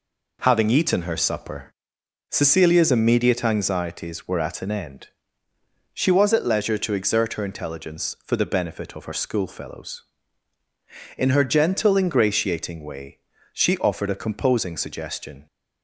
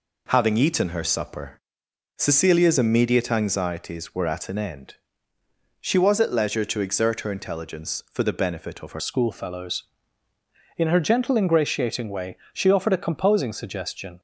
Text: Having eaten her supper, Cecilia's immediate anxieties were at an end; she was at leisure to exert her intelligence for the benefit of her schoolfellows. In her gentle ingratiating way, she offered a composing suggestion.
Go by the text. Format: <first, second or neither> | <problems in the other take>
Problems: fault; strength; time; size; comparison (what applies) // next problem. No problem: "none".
first | changes voice at "schoolfellows"; from 8.9 s on; 5.2 s long